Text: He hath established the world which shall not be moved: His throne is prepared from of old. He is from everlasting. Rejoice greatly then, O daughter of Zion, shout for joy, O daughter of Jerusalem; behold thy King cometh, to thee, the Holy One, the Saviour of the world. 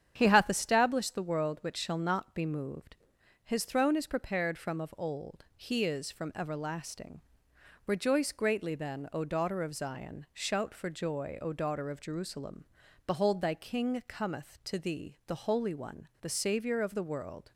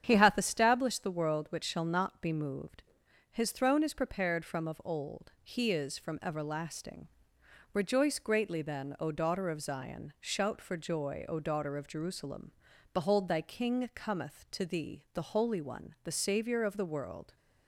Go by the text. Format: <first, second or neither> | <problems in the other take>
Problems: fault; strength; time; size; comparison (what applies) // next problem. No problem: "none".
neither | starts louder than the rest; strong; the same in both